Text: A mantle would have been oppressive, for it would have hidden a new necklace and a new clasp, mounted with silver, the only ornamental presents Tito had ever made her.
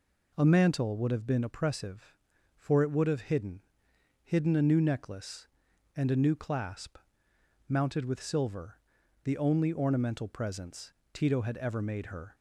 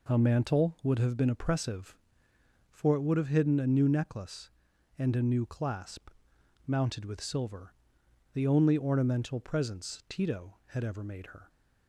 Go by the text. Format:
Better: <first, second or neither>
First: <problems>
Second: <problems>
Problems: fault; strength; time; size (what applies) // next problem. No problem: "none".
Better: second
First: says "hidden" twice; at 4.2 s // pauses between "presents" and "Tito"; slight; at 10.9 s; 0.22 s long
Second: none